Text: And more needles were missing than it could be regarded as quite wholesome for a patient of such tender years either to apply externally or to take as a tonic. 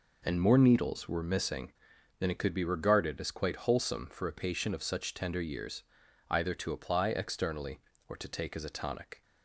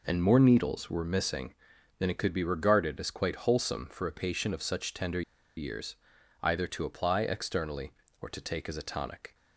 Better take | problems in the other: first | pauses between "tender" and "years"; at 5.2 s; 0.36 s long // pauses between "years" and "either"; at 5.9 s; 0.44 s long; also in the first

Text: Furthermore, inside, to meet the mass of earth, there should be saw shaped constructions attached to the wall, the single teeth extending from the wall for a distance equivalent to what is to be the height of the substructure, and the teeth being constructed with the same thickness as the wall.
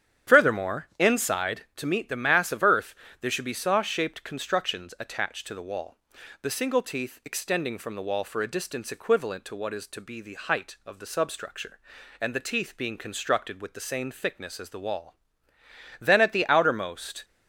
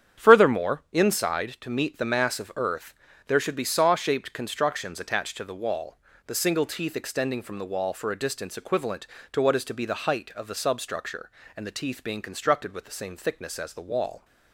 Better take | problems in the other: second | starts louder than the rest; strong; until 1.3 s; 9.5 dB; strong in the second // goes on to say "Then at the outermost"; noticeable; from 15.9 s on; 1.2 s long

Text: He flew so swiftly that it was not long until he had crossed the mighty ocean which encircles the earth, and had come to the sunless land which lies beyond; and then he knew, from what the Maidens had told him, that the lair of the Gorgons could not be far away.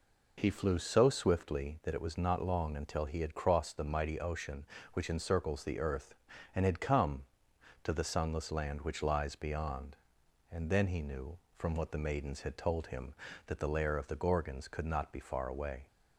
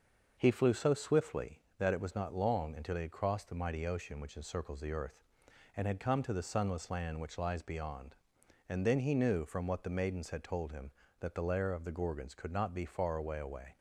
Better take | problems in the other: first | starts louder than the rest; noticeable; until 1.4 s; 6 dB // says "away" twice; at 13.3 s

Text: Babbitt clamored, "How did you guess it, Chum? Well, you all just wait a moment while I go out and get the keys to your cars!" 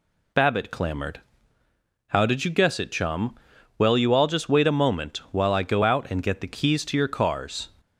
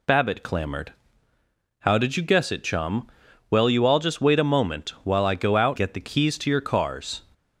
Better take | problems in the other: first | skips "and"; at 5.7 s

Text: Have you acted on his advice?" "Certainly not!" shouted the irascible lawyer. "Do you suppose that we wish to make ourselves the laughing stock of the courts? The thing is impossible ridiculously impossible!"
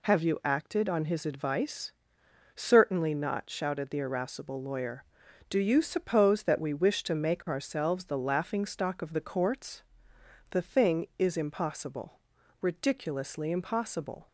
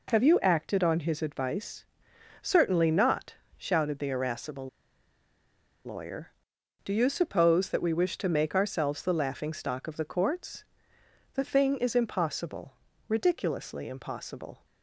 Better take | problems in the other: first | pauses between "irascible" and "lawyer"; at 4.6 s; 1.1 s long // pauses between "impossible" and "ridiculously"; slight; at 12.7 s; 0.34 s long; also in the first

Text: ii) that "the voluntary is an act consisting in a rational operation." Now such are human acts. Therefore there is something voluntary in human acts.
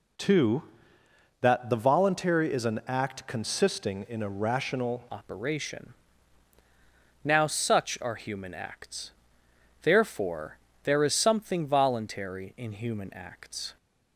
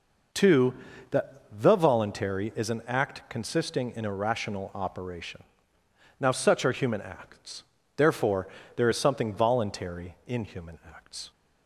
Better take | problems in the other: second | changes voice at "operation"; from 5.1 s on; 8.6 s long // pauses between "Therefore" and "there"; slight; at 10.5 s; 0.28 s long; slight in the second

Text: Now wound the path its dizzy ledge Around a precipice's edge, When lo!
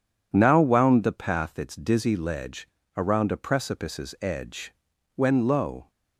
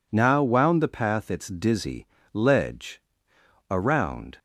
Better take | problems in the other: first | pauses between "dizzy" and "ledge"; slight; at 2.0 s; 0.26 s long // pauses between "ledge" and "Around"; noticeable; at 3.0 s; 0.68 s long; slight in the first // stops before "a precipice's edge When lo"; at 4.3 s

